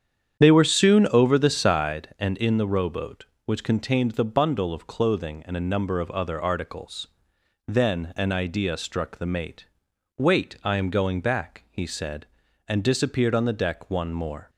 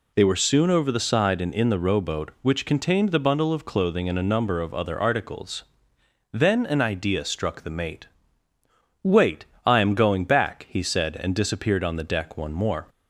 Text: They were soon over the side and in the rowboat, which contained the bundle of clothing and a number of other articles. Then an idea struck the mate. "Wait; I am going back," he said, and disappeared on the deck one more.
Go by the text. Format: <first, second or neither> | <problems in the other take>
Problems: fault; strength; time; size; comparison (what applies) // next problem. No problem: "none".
second | starts louder than the rest; strong; until 2.1 s; 8.5 dB